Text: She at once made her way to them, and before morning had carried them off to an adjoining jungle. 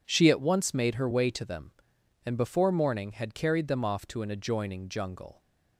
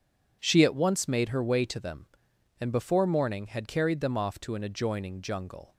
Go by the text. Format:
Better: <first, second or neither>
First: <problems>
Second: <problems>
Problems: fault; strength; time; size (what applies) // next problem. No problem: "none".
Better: neither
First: none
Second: none